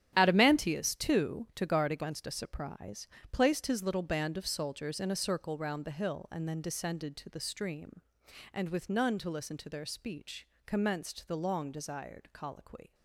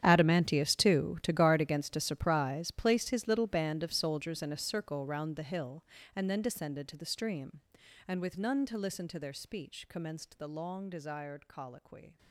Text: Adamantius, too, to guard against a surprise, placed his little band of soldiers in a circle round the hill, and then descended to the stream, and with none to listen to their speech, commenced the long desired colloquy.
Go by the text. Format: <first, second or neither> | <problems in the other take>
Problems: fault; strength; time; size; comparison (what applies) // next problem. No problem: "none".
first | gets quieter; strong; throughout; 18 dB // starts louder than the rest; strong; until 1.0 s; 9.5 dB; strong in the first